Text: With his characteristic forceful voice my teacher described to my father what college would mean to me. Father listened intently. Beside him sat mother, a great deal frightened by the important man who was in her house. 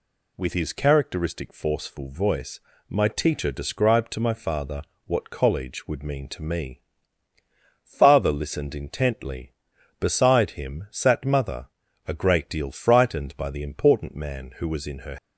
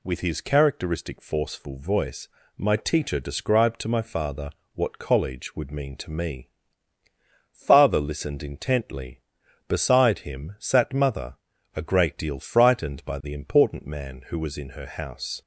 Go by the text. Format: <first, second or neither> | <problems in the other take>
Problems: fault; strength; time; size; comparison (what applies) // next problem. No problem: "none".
second | pauses between "voice" and "my"; slight; at 2.6 s; 0.28 s long; slight in the second // pauses between "father" and "what"; slight; at 4.8 s; 0.24 s long; slight in the second // stops before "house"; at 15.1 s